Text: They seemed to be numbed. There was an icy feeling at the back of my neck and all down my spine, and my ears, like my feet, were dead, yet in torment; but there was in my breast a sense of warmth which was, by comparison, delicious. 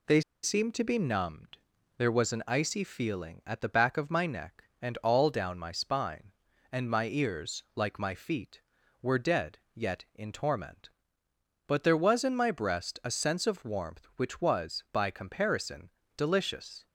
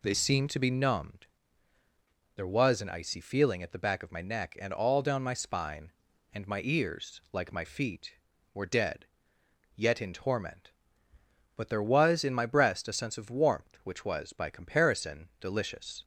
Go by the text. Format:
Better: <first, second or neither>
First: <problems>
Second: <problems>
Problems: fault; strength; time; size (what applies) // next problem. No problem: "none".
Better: second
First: pauses between "They" and "seemed"; slight; at 0.2 s; 0.22 s long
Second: none